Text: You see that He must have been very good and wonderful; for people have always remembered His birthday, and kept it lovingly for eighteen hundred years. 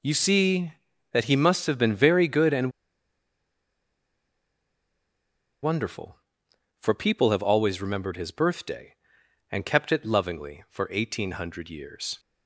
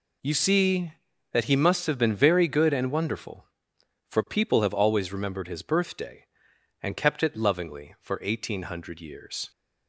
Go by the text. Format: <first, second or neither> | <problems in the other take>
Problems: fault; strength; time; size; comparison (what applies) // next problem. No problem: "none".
second | pauses between "and" and "wonderful"; strong; at 2.7 s; 2.9 s long